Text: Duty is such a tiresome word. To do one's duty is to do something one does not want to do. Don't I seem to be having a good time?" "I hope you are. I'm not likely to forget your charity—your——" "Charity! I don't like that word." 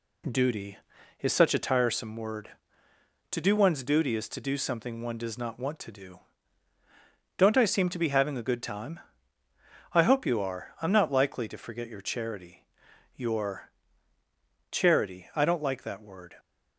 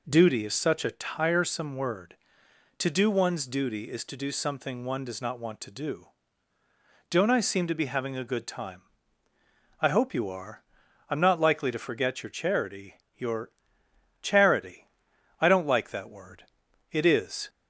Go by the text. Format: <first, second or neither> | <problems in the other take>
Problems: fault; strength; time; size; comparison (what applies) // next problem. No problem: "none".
first | goes on to say "It is"; from 16.9 s on; 0.56 s long